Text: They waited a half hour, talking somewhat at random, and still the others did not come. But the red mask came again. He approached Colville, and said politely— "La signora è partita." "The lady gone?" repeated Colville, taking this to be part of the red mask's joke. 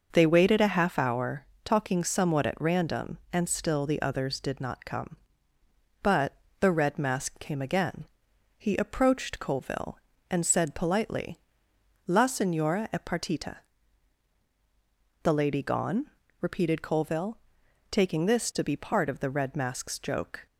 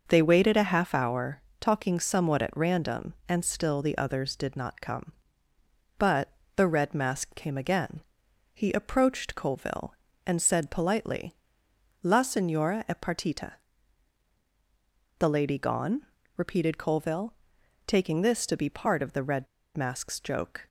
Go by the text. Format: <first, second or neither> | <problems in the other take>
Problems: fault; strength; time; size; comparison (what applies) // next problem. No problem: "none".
first | pauses between "But" and "the"; slight; at 6.3 s; 0.24 s long; slight in the first // pauses between "red" and "mask's"; slight; at 19.4 s; 0.30 s long